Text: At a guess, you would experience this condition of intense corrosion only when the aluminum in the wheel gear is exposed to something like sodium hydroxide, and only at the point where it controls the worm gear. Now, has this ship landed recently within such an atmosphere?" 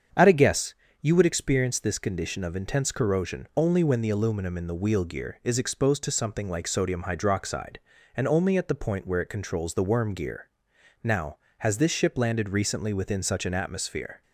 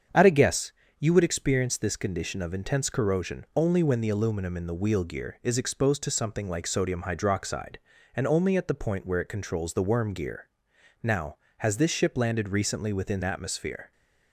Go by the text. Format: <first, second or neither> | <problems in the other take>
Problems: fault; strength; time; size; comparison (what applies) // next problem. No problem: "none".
first | starts louder than the rest; strong; until 1.4 s; 7.5 dB; strong in the first // skips "such an"; at 13.2 s